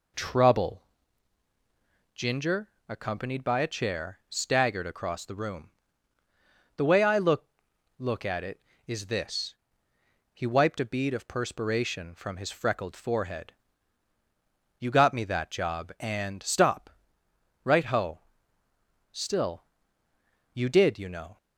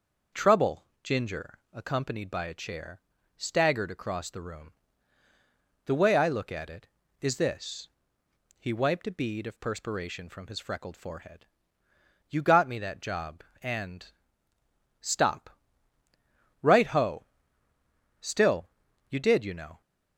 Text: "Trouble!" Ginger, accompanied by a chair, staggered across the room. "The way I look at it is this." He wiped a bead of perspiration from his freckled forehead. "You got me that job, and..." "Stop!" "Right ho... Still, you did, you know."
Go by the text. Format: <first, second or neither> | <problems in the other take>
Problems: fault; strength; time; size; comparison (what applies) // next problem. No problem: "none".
second | says "look" twice; at 7.9 s